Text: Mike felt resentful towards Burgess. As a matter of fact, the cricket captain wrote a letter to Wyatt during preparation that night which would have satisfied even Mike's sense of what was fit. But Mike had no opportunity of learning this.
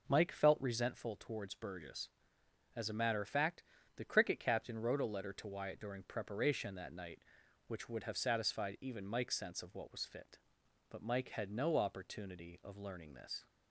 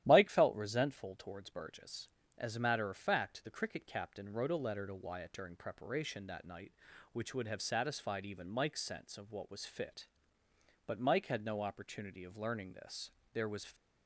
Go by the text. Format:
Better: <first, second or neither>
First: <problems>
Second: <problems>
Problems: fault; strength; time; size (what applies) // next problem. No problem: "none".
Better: first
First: none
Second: starts louder than the rest; strong; until 1.0 s; 12 dB // goes on to say "There was"; slight; from 13.3 s on; 0.42 s long